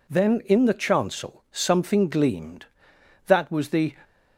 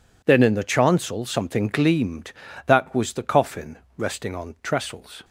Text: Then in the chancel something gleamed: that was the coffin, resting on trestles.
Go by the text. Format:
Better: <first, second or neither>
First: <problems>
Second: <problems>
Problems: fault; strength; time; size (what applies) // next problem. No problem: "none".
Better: second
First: stops before "coffin resting on trestles"; at 4.0 s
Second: none